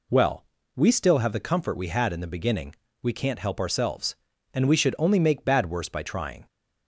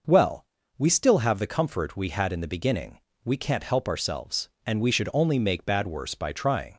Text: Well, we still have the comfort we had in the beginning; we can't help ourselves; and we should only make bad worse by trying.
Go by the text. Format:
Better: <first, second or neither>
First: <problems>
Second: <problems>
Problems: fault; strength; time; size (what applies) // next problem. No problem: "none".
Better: neither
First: none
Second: none